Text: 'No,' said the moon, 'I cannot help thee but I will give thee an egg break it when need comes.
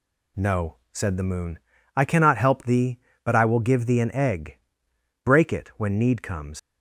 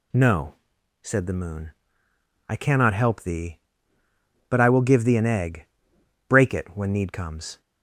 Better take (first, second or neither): second